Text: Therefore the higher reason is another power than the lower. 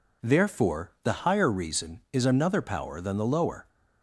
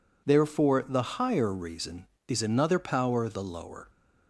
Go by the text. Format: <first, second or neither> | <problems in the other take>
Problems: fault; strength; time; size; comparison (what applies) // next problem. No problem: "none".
first | skips "than"; at 3.2 s